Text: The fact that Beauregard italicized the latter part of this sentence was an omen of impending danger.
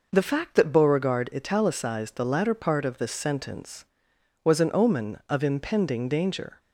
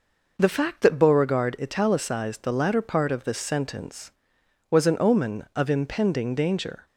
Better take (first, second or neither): neither